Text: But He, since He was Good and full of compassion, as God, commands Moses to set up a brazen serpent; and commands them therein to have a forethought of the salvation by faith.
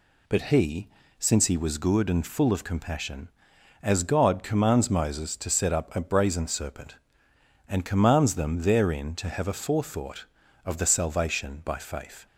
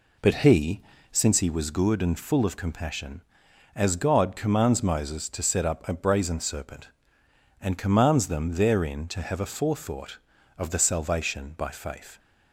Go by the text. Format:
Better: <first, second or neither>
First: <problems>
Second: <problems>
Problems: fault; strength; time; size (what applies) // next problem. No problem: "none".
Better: first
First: none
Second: starts louder than the rest; slight; until 1.3 s; 3 dB